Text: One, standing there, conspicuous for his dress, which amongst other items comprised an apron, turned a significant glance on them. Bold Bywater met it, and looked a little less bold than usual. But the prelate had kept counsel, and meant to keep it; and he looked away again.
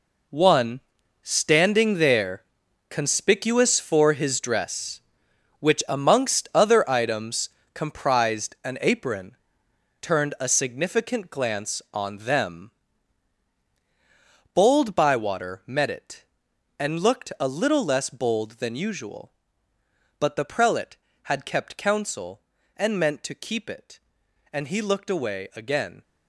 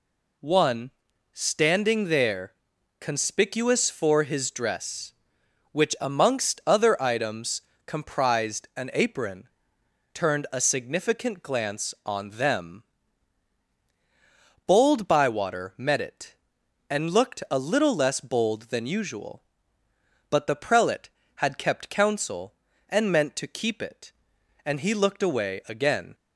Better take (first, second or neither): second